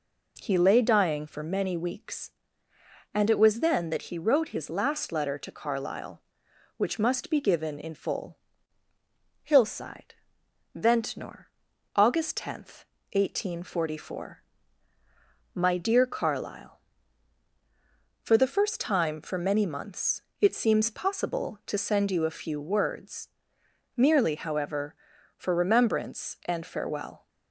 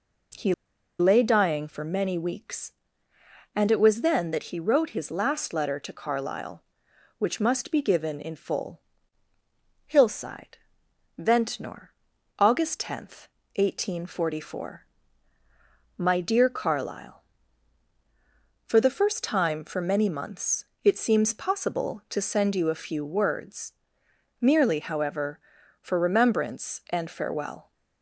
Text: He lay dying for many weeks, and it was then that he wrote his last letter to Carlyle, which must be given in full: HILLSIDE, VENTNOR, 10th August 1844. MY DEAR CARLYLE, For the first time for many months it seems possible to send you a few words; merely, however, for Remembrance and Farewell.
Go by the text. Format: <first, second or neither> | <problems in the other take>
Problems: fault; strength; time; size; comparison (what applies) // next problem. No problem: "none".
first | pauses between "He" and "lay"; noticeable; at 0.5 s; 0.46 s long // pauses between "months" and "it"; slight; at 20.6 s; 0.20 s long; slight in the first